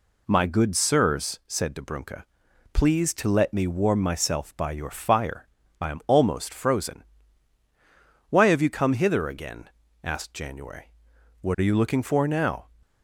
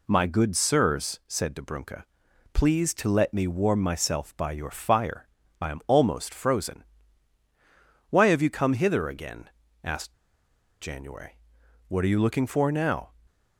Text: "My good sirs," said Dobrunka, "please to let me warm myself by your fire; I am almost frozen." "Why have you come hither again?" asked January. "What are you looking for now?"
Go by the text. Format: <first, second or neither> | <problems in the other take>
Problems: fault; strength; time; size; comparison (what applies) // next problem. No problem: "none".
first | pauses between "asked" and "January"; noticeable; at 10.1 s; 0.67 s long